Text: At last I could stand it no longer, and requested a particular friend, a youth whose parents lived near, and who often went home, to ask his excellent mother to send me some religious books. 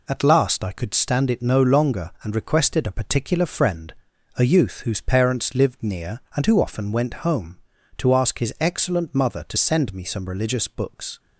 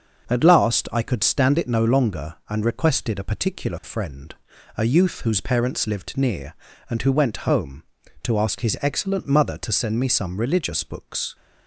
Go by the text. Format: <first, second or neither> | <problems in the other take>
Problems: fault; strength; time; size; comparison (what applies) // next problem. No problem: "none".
first | starts louder than the rest; until 1.3 s; 6.5 dB // skips "often"; at 7.1 s